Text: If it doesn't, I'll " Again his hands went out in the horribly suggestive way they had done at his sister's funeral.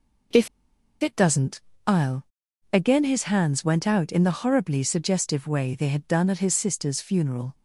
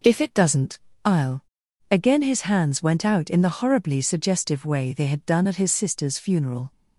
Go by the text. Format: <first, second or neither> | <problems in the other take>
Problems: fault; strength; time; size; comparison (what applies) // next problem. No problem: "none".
second | pauses between "If" and "it"; noticeable; at 0.4 s; 0.54 s long